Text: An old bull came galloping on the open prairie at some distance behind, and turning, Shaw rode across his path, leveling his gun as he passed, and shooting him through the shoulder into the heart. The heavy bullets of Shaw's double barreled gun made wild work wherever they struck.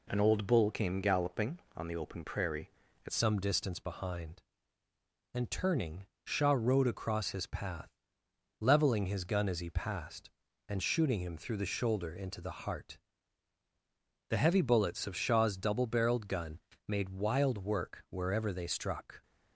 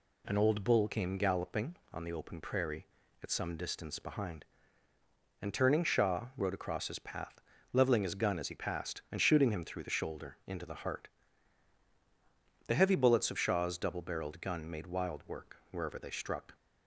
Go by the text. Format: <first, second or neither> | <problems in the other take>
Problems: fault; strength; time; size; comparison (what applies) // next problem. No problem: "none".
second | changes voice at "some"; from 3.1 s on; 16.1 s long // pauses between "gun" and "made"; slight; at 16.5 s; 0.26 s long